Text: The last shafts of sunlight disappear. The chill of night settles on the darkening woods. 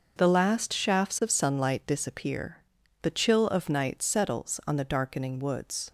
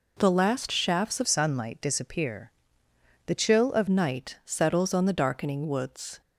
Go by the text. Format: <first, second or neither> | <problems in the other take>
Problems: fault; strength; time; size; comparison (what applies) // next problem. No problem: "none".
first | changes voice from "sunlight" to "of"; from 1.2 to 3.8 s; 2.6 s long